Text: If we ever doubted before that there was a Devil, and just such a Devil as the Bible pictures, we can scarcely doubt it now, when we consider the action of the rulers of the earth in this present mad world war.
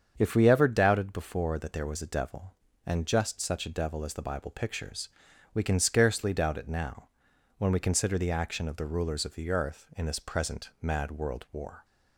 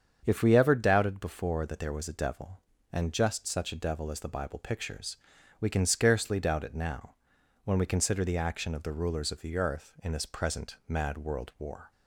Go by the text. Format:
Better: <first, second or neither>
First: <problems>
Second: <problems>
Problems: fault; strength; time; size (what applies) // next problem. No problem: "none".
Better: neither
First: starts louder than the rest; strong; until 1.1 s; 7.5 dB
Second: starts louder than the rest; strong; until 1.2 s; 7.5 dB